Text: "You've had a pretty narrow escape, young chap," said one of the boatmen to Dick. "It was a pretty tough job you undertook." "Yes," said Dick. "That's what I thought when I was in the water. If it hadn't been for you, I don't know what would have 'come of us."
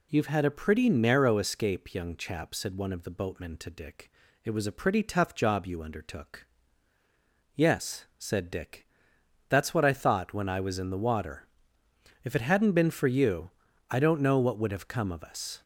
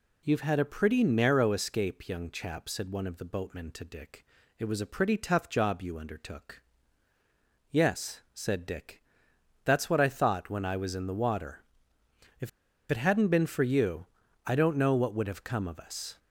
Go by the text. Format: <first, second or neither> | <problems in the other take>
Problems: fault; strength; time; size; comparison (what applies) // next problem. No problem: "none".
first | pauses between "If" and "it"; at 12.4 s; 0.42 s long